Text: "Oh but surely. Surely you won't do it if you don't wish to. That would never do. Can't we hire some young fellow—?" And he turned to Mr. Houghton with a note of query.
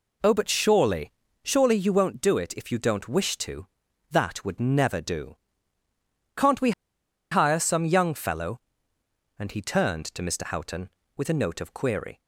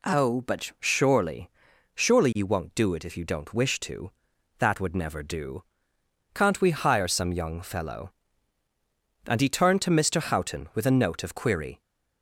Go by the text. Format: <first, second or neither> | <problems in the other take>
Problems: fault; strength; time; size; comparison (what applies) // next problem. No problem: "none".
second | pauses between "we" and "hire"; noticeable; at 6.7 s; 0.60 s long